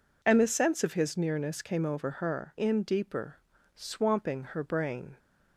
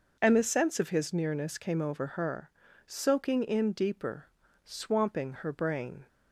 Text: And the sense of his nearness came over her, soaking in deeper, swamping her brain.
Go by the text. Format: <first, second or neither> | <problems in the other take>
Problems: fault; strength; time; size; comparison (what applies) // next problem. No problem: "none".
second | skips "soaking"; at 2.5 s